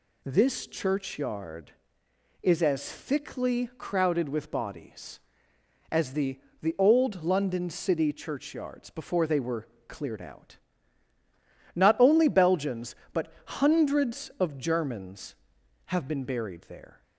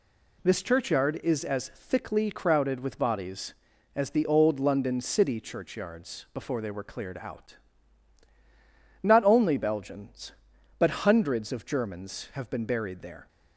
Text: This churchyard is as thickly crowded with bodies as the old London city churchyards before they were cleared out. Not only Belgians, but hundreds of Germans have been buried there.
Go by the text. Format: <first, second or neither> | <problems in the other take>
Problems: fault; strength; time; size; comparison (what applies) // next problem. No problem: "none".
second | says "the" twice; at 6.6 s // pauses between "were" and "cleared"; slight; at 9.6 s; 0.22 s long